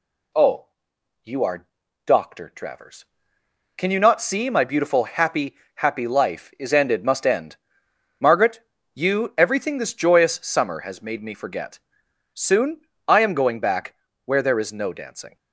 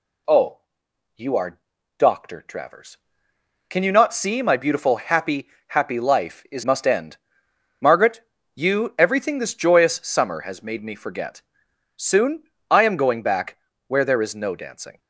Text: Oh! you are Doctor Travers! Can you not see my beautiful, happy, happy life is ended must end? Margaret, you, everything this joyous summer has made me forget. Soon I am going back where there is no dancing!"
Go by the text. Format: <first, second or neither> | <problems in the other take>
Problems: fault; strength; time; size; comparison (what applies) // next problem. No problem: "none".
first | pauses between "are" and "Doctor"; at 1.6 s; 0.38 s long; also in the first // skips "ended"; at 6.6 s // pauses between "Soon" and "I"; slight; at 12.4 s; 0.28 s long; slight in the first // pauses between "back" and "where"; slight; at 13.5 s; 0.30 s long; slight in the first